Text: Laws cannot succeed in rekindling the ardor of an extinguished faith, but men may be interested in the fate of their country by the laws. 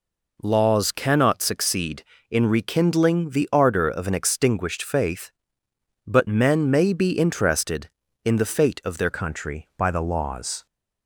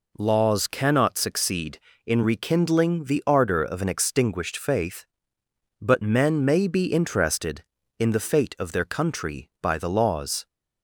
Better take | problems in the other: second | changes voice at "country"; from 9.1 s on; 1.5 s long

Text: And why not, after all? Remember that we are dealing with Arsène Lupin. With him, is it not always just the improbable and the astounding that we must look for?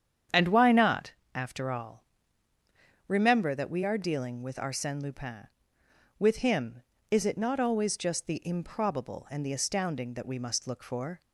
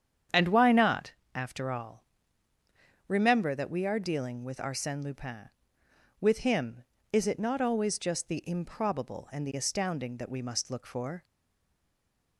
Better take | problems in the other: first | starts louder than the rest; strong; until 1.5 s; 8.5 dB; strong in the first // stays silent after the last word; noticeable; from 11.2 s on; 1.1 s long

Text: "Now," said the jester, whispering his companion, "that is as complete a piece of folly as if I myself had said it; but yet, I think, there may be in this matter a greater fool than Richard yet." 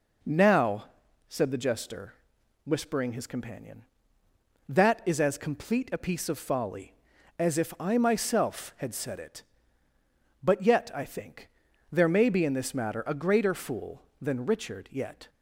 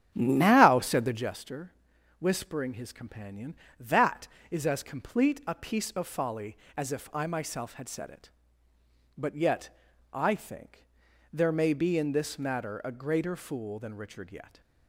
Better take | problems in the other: first | starts louder than the rest; strong; until 1.4 s; 9 dB

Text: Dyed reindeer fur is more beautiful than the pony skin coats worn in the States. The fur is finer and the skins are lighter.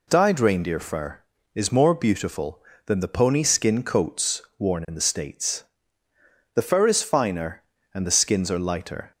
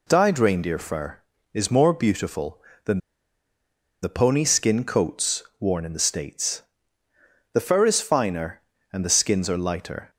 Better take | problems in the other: first | pauses between "than" and "the"; at 2.9 s; 1.0 s long // pauses between "coats" and "worn"; slight; at 5.4 s; 0.16 s long; slight in the first

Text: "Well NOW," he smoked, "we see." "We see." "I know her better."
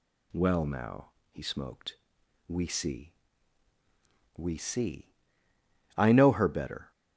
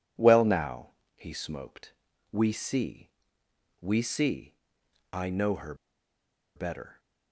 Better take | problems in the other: first | pauses between "her" and "better"; noticeable; at 5.7 s; 0.81 s long

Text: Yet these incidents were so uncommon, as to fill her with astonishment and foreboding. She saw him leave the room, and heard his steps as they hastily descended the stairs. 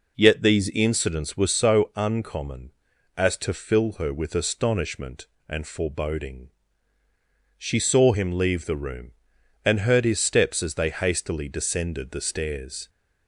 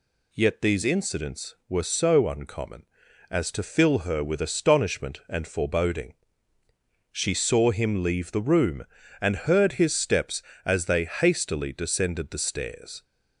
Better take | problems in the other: neither | none

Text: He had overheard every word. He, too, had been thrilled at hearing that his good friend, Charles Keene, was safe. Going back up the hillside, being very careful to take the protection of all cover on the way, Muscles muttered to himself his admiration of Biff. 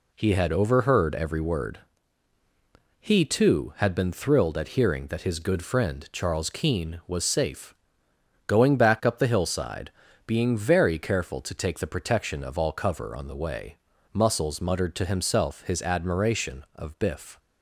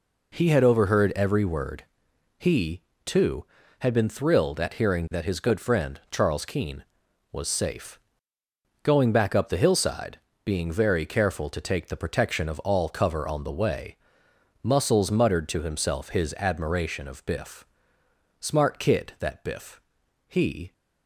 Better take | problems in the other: first | goes on to say "Smart kid that Biff he"; strong; from 18.3 s on; 2.3 s long

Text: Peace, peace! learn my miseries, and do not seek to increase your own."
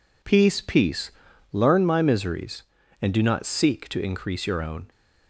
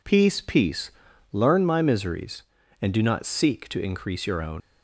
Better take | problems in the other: first | leaves "own" unfinished; at 4.6 s; 95 ms

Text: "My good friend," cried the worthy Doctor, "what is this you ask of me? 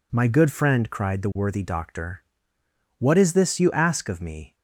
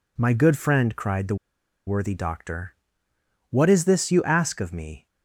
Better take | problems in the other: first | pauses between "the" and "worthy"; noticeable; at 1.3 s; 0.51 s long

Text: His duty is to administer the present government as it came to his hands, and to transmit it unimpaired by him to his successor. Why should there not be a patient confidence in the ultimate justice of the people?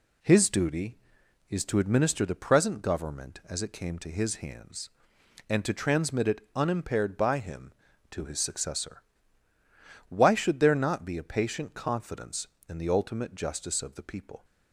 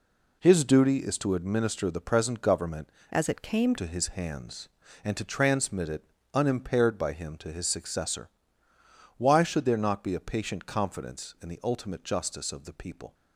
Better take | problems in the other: first | changes voice from "as" to "came"; from 3.1 to 3.7 s; 0.6 s long // pauses between "it" and "unimpaired"; slight; at 6.0 s; 0.30 s long

